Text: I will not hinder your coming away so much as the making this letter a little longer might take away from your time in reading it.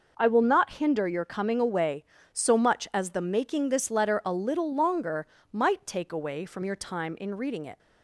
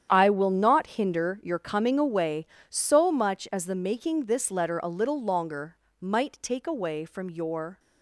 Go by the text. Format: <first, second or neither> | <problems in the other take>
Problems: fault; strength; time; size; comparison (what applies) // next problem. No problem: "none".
first | starts louder than the rest; strong; until 1.1 s; 9 dB // pauses between "longer" and "might"; slight; at 5.7 s; 0.24 s long; slight in the first // stops before "time in reading it"; at 7.7 s